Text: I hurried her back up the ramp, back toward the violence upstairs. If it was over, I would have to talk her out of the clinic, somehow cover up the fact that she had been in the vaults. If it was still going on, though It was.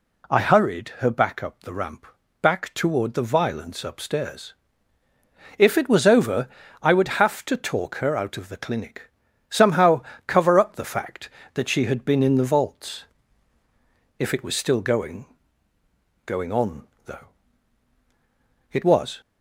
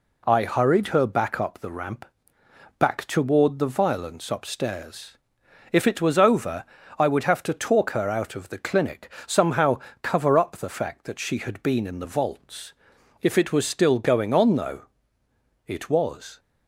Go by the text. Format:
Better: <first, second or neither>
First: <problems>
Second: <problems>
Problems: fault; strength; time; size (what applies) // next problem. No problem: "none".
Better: second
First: pauses between "somehow" and "cover"; slight; at 10.0 s; 0.24 s long // says "going" twice; at 16.2 s // pauses between "though" and "It"; strong; at 17.2 s; 1.4 s long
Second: pauses between "somehow" and "cover"; slight; at 9.7 s; 0.22 s long // pauses between "though" and "It"; noticeable; at 14.8 s; 0.84 s long